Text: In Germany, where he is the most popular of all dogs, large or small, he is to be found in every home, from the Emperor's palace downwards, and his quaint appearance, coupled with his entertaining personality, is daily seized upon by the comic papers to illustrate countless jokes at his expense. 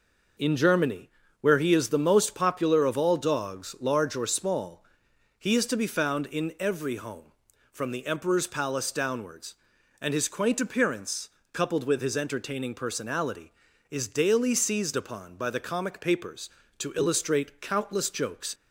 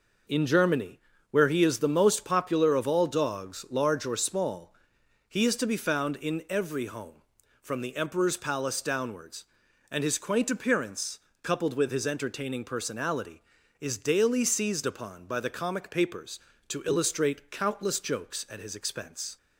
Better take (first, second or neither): second